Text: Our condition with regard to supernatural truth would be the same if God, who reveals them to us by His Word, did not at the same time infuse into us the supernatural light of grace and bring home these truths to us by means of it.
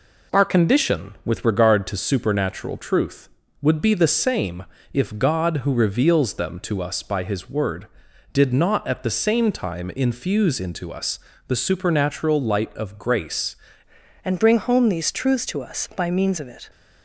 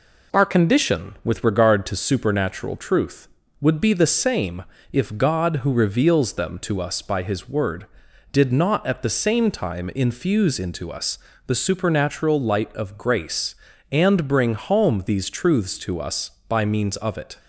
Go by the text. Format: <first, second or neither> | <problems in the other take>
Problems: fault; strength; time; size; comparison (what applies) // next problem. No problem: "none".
second | pauses between "same" and "if"; slight; at 4.6 s; 0.30 s long; slight in the second // pauses between "us" and "the"; slight; at 11.1 s; 0.30 s long; slight in the second // changes voice at "and"; from 14.2 s on; 2.4 s long